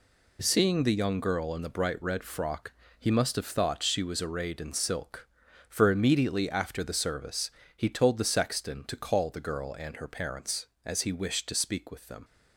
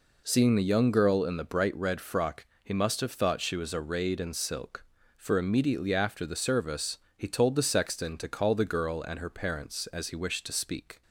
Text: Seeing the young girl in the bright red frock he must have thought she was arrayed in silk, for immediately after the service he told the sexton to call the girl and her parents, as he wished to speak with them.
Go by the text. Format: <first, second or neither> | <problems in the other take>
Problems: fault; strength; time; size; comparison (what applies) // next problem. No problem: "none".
first | pauses between "frock" and "he"; slight; at 2.4 s; 0.18 s long; slight in the first // pauses between "service" and "he"; slight; at 6.9 s; 0.20 s long; slight in the first // stops before "with them"; at 11.0 s